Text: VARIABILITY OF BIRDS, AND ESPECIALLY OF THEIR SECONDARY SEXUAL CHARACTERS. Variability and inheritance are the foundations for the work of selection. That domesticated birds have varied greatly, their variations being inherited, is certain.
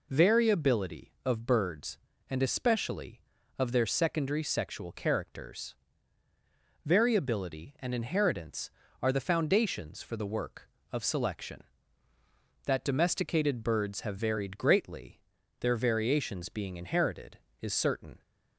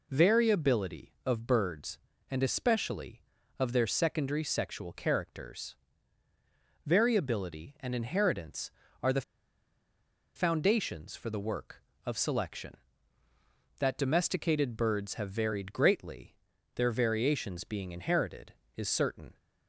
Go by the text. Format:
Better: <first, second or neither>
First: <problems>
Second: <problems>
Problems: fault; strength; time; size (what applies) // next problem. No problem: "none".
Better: first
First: none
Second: pauses between "the" and "foundations"; at 9.2 s; 1.1 s long